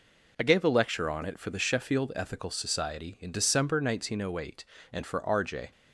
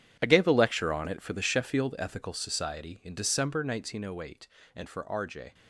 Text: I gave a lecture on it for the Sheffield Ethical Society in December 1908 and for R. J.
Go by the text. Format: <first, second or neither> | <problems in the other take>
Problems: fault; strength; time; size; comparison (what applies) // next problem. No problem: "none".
first | gets quieter; strong; throughout; 14 dB